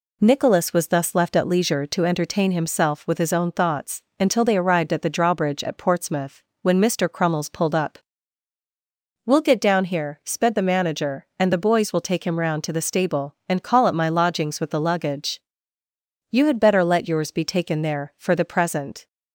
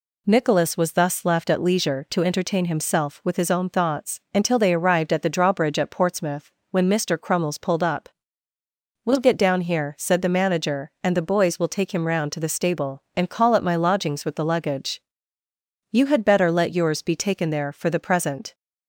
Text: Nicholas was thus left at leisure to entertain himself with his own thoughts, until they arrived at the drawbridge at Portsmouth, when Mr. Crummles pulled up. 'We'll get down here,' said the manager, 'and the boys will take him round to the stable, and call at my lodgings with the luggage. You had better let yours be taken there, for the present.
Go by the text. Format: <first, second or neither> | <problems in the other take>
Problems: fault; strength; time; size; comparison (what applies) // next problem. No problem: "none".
second | says "sped" for "said"; at 10.2 s